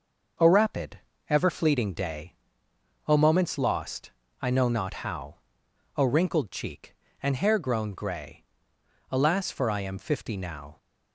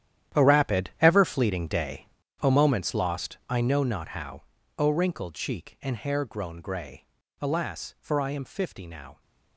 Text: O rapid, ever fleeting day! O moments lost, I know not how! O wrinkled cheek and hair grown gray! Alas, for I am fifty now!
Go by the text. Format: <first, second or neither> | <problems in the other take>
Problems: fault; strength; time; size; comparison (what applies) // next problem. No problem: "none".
first | gets quieter; strong; throughout; 14.5 dB